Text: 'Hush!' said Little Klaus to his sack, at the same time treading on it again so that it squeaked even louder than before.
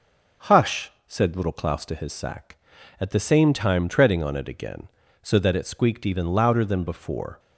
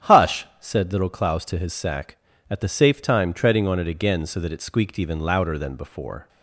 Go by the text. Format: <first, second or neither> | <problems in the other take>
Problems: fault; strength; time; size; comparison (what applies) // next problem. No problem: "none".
first | starts louder than the rest; strong; until 1.1 s; 10 dB; also in the first // says "safe" for "same"; at 2.6 s